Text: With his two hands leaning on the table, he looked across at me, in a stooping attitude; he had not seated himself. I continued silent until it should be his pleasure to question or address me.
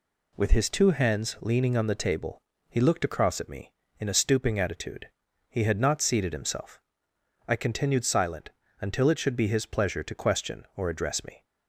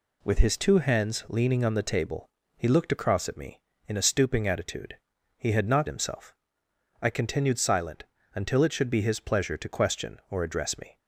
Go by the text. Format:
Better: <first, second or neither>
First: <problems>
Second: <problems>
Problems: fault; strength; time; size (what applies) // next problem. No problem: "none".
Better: first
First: pauses between "silent" and "until"; slight; at 8.4 s; 0.32 s long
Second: skips "seated"; at 5.8 s // pauses between "silent" and "until"; slight; at 8.0 s; 0.32 s long